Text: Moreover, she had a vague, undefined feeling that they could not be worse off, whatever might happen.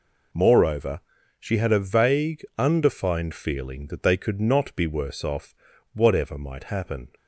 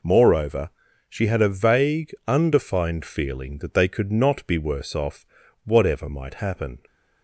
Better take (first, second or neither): neither